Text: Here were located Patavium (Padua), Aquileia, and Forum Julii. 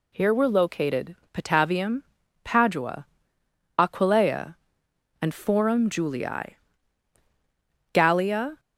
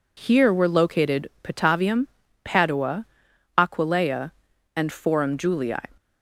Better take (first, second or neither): second